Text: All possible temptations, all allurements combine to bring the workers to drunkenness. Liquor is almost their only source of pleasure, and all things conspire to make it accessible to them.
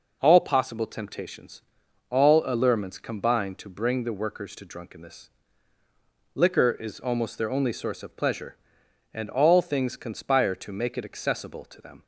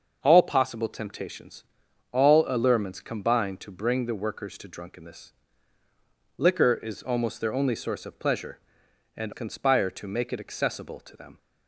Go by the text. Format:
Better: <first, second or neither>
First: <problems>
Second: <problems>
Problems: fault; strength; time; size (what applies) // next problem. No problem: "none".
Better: first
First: none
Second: starts louder than the rest; until 1.2 s; 6.5 dB // skips "all things"; at 9.3 s